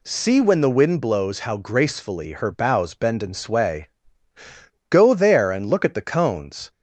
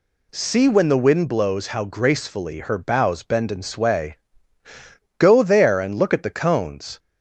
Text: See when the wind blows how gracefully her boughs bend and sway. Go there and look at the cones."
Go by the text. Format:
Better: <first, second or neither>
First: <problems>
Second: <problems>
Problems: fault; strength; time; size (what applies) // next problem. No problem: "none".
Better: neither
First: none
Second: none